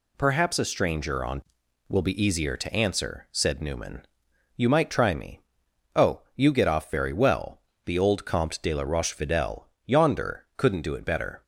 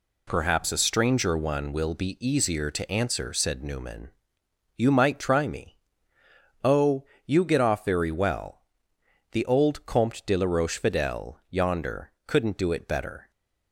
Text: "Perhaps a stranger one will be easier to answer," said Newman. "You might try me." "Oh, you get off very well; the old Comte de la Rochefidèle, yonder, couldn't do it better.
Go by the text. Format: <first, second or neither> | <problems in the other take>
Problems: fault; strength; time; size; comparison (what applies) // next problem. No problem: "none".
second | says "on" for "one"; at 1.2 s